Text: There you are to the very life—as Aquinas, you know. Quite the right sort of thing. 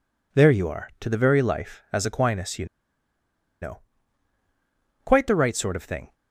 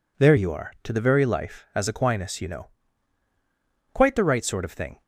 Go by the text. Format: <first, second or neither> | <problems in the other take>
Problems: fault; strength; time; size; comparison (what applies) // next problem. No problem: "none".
second | pauses between "you" and "know"; noticeable; at 2.6 s; 0.96 s long